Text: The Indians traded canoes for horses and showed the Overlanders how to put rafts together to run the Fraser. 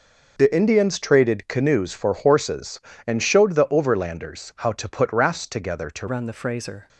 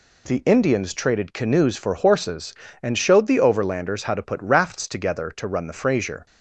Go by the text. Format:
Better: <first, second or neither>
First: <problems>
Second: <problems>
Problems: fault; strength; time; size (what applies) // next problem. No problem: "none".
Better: second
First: changes voice at "run"; from 6.0 s on; 0.8 s long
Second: none